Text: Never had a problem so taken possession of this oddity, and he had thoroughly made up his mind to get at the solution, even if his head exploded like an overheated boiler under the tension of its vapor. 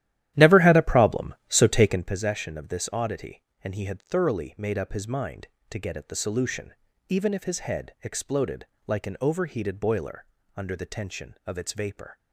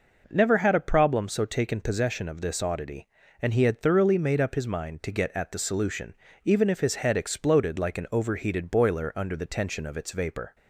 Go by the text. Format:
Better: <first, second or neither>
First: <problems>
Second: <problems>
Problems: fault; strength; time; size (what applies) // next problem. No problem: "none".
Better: second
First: starts louder than the rest; strong; until 2.2 s; 13 dB // pauses between "exploded" and "like"; slight; at 8.6 s; 0.22 s long // pauses between "boiler" and "under"; slight; at 10.2 s; 0.30 s long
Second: none